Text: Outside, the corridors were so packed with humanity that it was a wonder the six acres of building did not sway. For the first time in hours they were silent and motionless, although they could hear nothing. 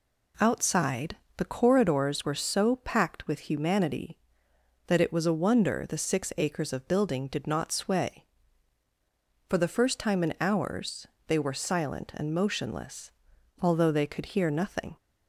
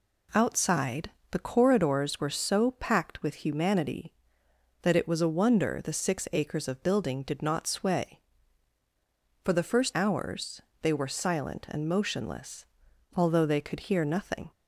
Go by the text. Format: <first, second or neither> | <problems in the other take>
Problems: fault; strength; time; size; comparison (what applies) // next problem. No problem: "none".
first | skips "time in"; at 9.9 s // pauses between "hours" and "they"; slight; at 10.6 s; 0.22 s long; slight in the first